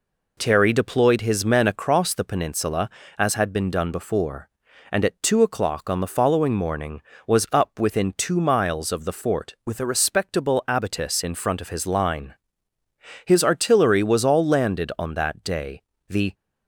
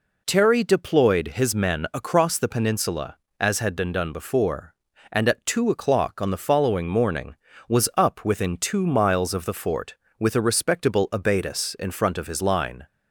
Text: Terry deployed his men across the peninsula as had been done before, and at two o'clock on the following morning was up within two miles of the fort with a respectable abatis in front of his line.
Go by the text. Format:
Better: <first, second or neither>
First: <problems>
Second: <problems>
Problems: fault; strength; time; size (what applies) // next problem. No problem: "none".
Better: second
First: goes on to say "His artillery was all landed on that day the"; strong; from 13.2 s on; 3.0 s long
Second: none